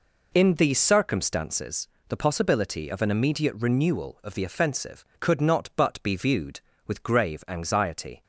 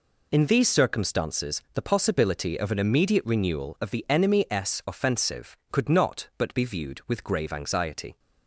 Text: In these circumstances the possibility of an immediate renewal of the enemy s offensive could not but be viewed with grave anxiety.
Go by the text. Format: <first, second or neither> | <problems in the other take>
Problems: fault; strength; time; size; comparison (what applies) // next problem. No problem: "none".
second | pauses between "circumstances" and "the"; slight; at 1.8 s; 0.22 s long // skips "enemy s"; at 4.4 s